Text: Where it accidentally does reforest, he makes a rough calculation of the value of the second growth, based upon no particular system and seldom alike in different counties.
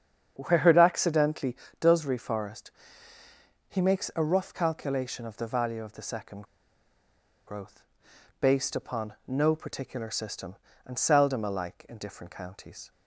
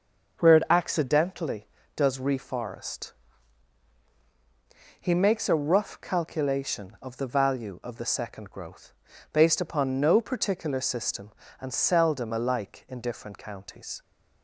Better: second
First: starts louder than the rest; strong; until 1.3 s; 8 dB // pauses between "second" and "growth"; at 6.4 s; 1.0 s long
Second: starts louder than the rest; noticeable; until 1.4 s; 6 dB

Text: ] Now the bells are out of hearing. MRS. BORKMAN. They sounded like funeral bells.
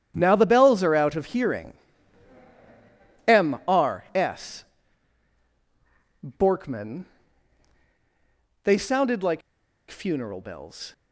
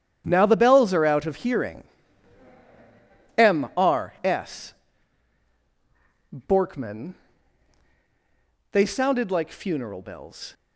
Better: second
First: starts louder than the rest; strong; until 1.1 s; 9.5 dB // pauses between "like" and "funeral"; noticeable; at 9.4 s; 0.49 s long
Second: starts louder than the rest; strong; until 1.2 s; 10 dB

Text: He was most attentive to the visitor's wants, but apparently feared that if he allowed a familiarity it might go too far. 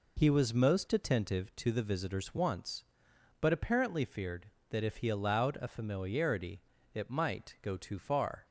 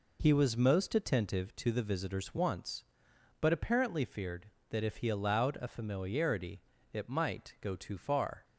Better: neither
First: pauses between "familiarity" and "it"; slight; at 6.5 s; 0.34 s long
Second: pauses between "familiarity" and "it"; slight; at 6.5 s; 0.32 s long

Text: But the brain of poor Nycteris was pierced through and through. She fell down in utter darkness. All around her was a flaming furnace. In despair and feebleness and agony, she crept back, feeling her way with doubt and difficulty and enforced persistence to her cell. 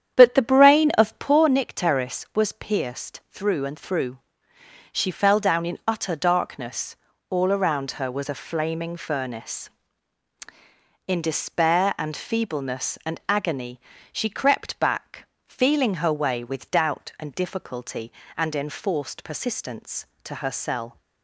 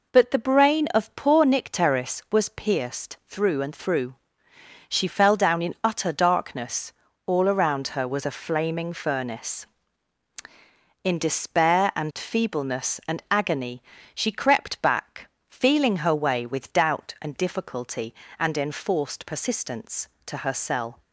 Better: second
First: starts louder than the rest; strong; until 1.4 s; 9 dB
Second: none

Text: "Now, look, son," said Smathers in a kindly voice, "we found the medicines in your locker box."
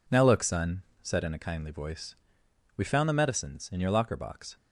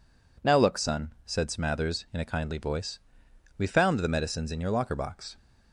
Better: second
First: skips "Smathers"; at 1.2 s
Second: none

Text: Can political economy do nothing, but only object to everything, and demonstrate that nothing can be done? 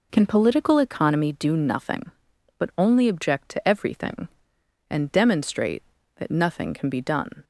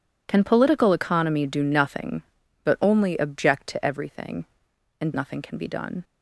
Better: first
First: none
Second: skips "demonstrate that"; at 5.1 s

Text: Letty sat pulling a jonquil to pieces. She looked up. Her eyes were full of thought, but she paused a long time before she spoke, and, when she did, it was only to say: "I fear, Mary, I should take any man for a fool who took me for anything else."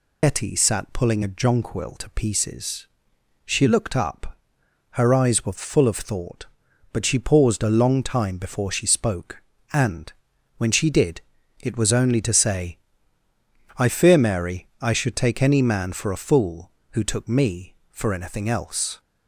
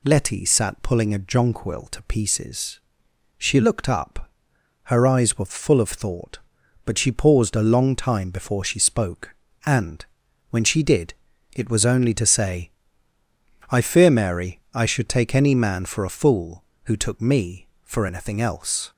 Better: second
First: loses the start of "Letty"; at 0.2 s; 85 ms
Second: none

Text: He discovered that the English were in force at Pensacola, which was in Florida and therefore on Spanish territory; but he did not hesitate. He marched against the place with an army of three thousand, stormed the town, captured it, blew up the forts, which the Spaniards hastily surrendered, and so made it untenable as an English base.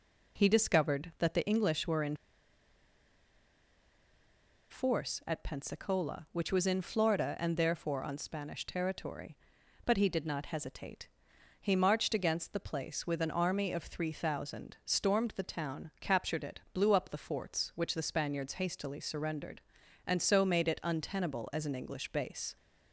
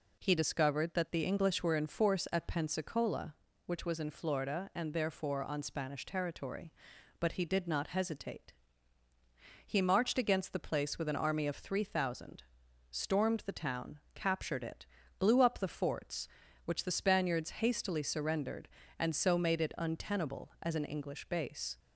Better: second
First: pauses between "in" and "force"; strong; at 2.1 s; 2.5 s long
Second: none

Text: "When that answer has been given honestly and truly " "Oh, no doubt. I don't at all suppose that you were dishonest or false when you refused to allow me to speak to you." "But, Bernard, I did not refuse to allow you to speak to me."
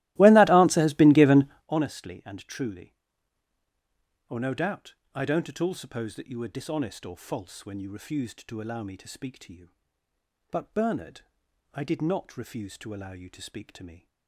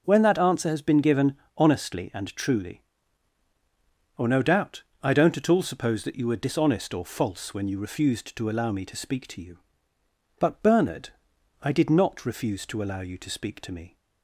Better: second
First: starts louder than the rest; strong; until 1.7 s; 17 dB // pauses between "given" and "honestly"; slight; at 1.4 s; 0.22 s long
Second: pauses between "given" and "honestly"; slight; at 1.3 s; 0.22 s long

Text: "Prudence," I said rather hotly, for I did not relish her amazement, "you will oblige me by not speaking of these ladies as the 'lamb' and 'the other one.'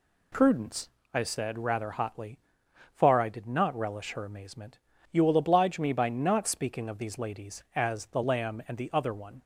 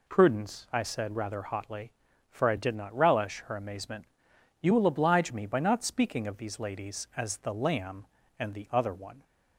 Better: second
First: says "far" for "for"; at 2.9 s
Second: none

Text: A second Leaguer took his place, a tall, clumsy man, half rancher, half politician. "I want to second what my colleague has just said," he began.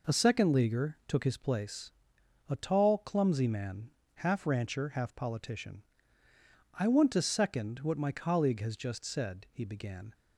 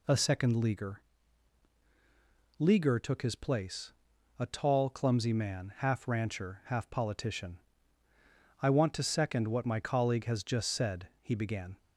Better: first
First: none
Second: says "Leaguer" twice; at 2.5 s

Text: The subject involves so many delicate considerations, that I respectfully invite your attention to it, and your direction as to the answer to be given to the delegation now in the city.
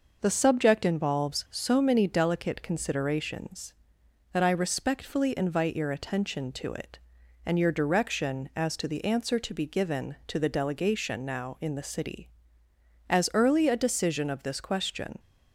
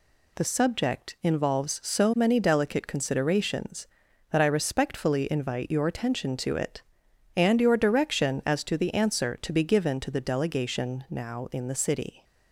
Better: second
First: goes on to say "As early a decision of this question"; strong; from 13.0 s on; 2.1 s long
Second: none

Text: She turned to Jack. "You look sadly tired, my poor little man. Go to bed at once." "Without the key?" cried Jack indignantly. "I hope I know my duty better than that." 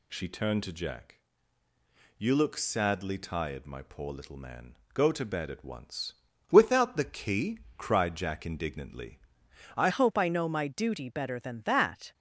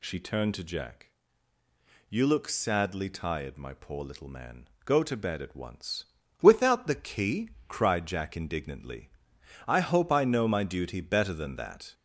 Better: second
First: changes voice at "hope"; from 9.8 s on; 2.3 s long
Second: none

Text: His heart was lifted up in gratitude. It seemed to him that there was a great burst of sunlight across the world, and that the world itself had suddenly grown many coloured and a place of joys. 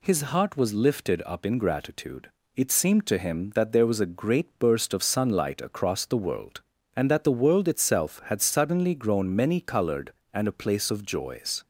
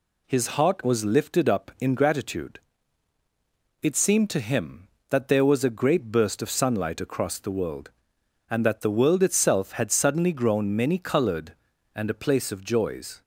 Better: neither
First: none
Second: none

